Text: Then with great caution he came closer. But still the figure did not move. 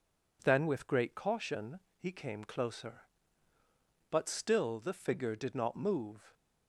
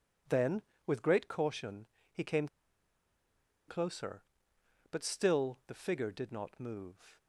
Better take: first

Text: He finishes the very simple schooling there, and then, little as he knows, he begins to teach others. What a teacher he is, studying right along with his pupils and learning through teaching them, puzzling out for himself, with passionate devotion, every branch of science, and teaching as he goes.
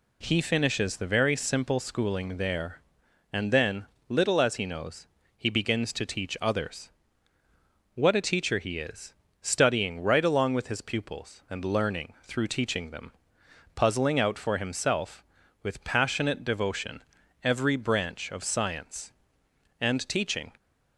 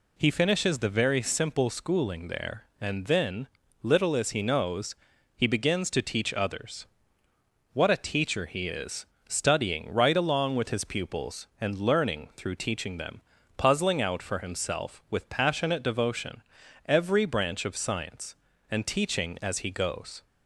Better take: second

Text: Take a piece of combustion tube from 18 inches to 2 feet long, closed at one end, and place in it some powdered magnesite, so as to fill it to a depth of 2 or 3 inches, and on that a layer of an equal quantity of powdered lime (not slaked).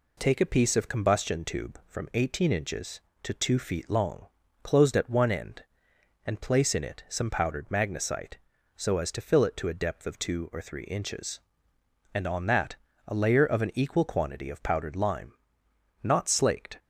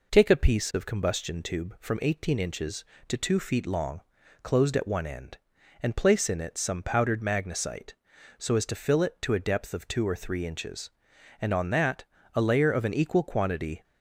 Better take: first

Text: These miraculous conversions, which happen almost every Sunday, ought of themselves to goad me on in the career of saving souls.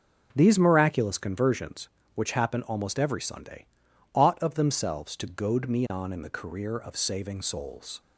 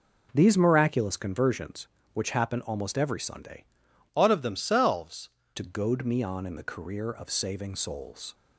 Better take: first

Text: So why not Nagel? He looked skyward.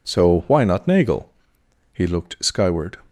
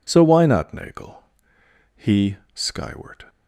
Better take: first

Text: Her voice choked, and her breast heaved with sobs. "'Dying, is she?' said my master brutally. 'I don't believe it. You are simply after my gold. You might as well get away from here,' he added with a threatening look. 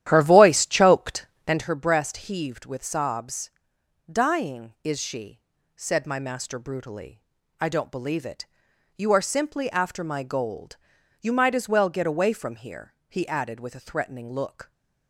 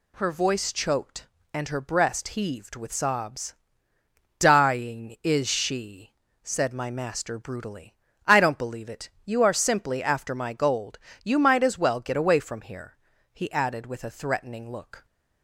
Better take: second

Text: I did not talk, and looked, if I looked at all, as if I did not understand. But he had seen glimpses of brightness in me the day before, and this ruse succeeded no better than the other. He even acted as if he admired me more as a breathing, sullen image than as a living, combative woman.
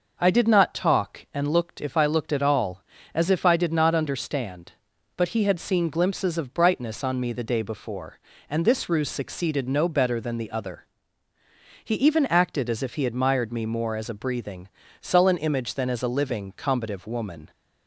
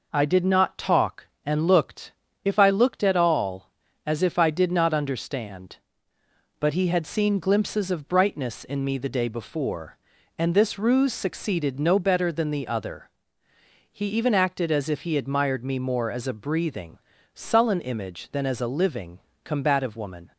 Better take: second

